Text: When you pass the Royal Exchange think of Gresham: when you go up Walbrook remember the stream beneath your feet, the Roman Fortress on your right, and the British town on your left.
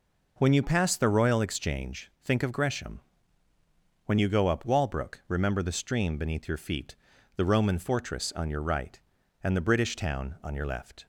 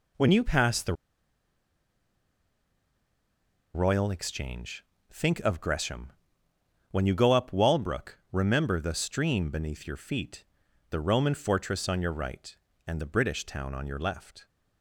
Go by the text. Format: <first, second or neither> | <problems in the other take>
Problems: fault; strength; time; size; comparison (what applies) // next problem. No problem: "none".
first | pauses between "the" and "Royal"; strong; at 0.9 s; 2.8 s long // pauses between "Exchange" and "think"; slight; at 4.8 s; 0.28 s long